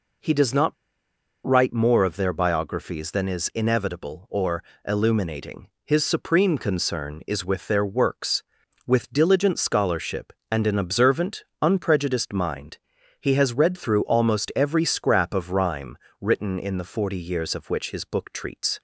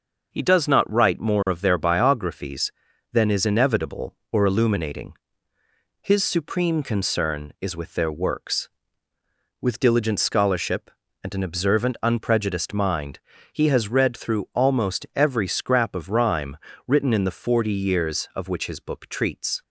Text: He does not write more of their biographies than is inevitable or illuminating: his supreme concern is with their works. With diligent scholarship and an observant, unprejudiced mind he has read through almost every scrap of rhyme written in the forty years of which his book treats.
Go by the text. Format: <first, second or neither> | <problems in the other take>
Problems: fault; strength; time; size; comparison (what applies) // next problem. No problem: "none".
second | pauses between "not" and "write"; noticeable; at 0.7 s; 0.71 s long // pauses between "or" and "illuminating"; slight; at 4.6 s; 0.20 s long // pauses between "mind" and "he"; at 12.7 s; 0.42 s long; slight in the second // pauses between "rhyme" and "written"; slight; at 15.9 s; 0.24 s long; slight in the second